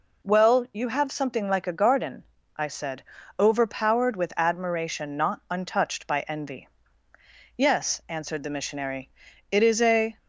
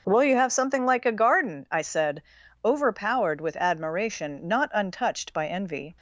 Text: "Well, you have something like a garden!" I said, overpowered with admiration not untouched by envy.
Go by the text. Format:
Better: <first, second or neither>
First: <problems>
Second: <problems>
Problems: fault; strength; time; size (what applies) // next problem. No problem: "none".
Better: second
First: goes on to say "Yes answered the missionary it is a"; strong; from 7.5 s on; 2.6 s long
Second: none